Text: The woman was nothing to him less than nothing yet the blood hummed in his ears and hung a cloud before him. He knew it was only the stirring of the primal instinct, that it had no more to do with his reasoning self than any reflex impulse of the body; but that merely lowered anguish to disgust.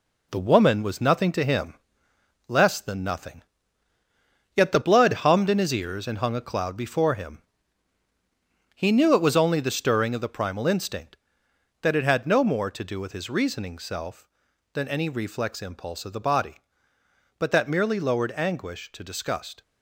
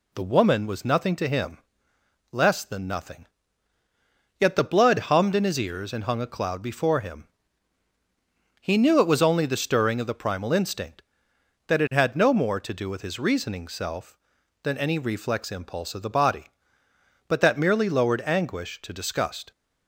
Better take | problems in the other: second | gets quieter; noticeable; throughout; 5.5 dB // pauses between "him" and "less"; noticeable; at 1.7 s; 0.74 s long; noticeable in the second // pauses between "nothing" and "yet"; at 3.4 s; 1.1 s long; also in the second

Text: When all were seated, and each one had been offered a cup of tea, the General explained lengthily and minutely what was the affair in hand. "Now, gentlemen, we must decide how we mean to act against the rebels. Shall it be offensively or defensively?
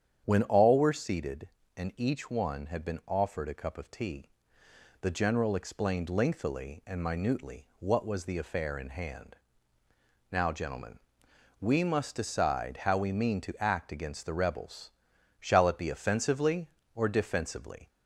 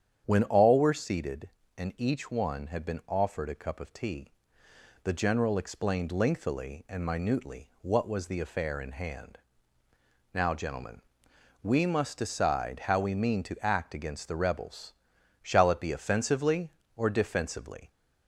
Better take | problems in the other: neither | starts louder than the rest; strong; the same in both

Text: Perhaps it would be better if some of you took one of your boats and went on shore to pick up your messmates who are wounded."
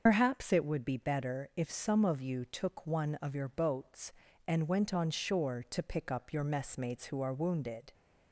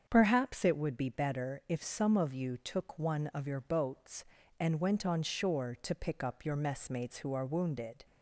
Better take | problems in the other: second | loses the start of "Perhaps"; at 0.0 s; 85 ms // starts louder than the rest; until 1.0 s; 6.5 dB; strong in the second

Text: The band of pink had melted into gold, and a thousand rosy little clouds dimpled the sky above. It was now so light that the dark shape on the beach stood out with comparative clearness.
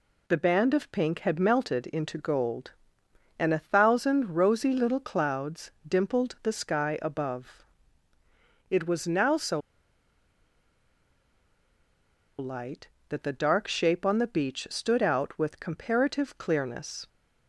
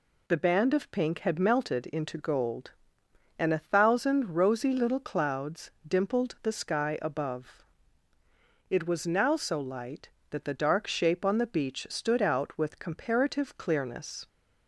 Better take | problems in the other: second | pauses between "clouds" and "dimpled"; slight; at 5.7 s; 0.16 s long; slight in the second // pauses between "so" and "light"; strong; at 9.6 s; 2.7 s long

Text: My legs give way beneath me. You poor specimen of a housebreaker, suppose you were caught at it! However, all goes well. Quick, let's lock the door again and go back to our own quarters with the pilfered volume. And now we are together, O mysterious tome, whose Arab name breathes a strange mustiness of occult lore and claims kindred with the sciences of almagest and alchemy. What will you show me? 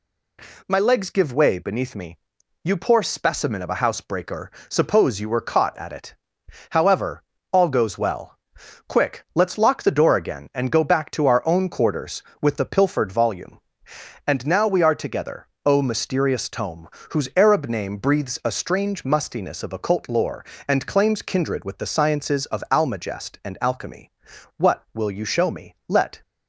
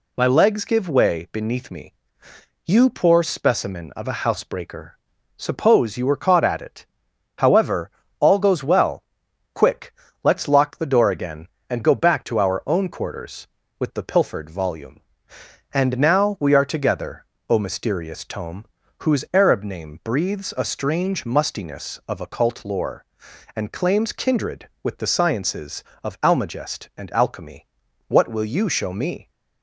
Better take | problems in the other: second | goes on to say "Let"; slight; from 25.8 s on; 0.32 s long

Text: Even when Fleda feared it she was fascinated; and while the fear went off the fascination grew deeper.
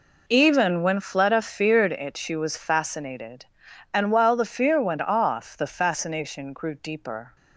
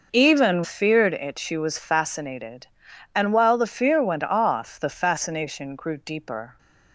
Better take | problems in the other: first | skips "when Fleda"; at 0.6 s

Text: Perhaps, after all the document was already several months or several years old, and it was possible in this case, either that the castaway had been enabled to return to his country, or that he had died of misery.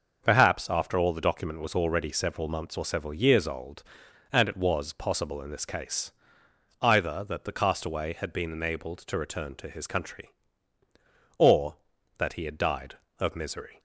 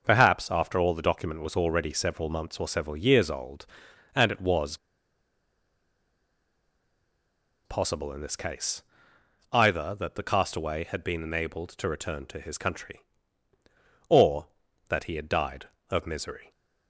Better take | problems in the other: first | pauses between "was" and "possible"; strong; at 4.7 s; 2.8 s long

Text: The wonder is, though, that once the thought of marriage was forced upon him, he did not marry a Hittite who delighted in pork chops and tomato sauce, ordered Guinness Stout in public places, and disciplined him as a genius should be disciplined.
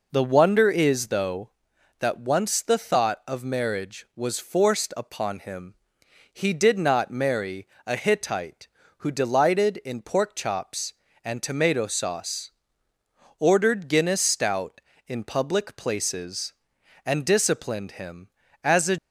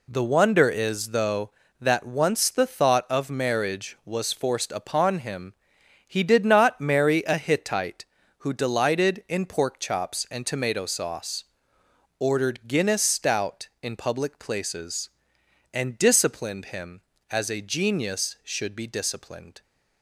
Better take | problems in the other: second | pauses between "marry" and "a"; slight; at 7.6 s; 0.18 s long // stops before "genius should be disciplined"; at 18.9 s

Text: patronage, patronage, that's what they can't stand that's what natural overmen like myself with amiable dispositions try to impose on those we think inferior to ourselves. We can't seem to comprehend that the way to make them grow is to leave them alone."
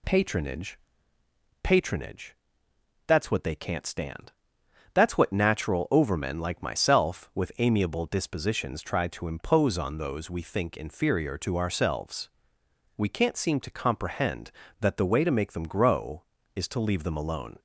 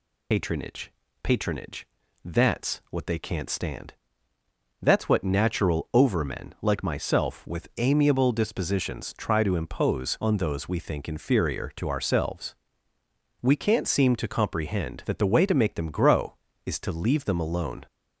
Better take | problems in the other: first | loses the start of "patronage"; at 0.3 s; 70 ms // pauses between "stand" and "that's"; noticeable; at 3.9 s; 0.88 s long; noticeable in the first

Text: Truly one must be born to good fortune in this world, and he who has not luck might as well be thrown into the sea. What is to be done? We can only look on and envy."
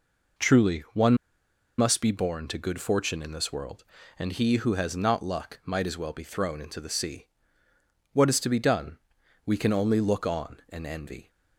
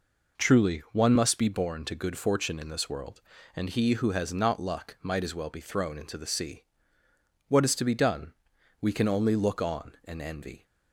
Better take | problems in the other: second | pauses between "one" and "must"; noticeable; at 1.1 s; 0.64 s long

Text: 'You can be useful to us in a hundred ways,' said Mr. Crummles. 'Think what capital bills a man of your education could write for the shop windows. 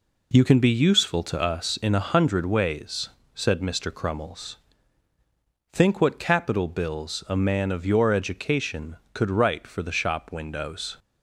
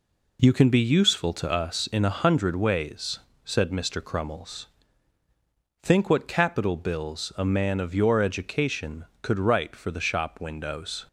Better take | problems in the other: neither | none

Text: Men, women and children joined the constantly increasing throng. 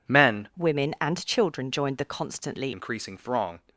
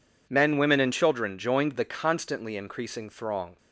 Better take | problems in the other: second | changes voice from "women" to "constantly"; from 0.5 to 2.7 s; 2.2 s long

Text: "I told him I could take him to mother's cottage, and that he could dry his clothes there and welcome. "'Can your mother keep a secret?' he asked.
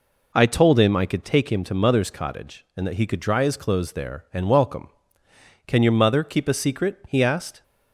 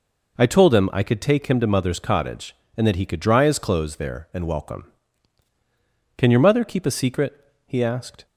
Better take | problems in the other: neither | none

